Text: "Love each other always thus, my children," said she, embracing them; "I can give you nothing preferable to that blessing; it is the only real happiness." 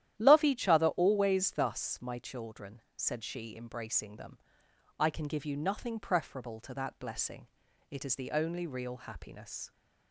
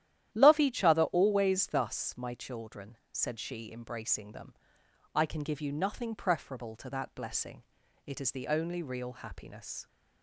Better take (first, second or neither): neither